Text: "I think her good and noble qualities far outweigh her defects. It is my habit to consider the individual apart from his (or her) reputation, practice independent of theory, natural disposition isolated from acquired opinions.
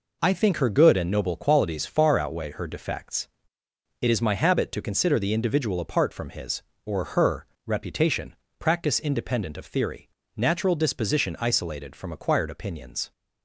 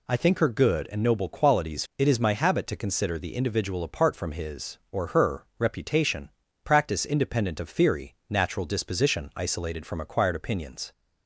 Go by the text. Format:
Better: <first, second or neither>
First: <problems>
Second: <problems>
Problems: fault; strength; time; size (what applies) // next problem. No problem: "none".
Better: first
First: none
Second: skips "far outweigh her defects"; at 1.9 s